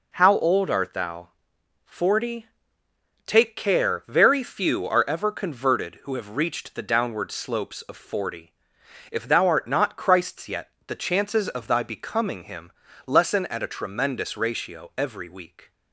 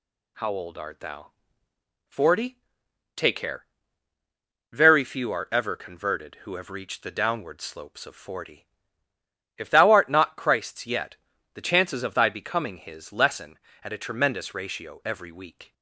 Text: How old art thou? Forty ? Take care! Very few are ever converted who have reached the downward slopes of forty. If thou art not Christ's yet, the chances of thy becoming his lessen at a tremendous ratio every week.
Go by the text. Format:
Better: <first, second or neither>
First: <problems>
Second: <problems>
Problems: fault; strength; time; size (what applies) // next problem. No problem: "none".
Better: second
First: says "him" for "his"; at 12.4 s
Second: none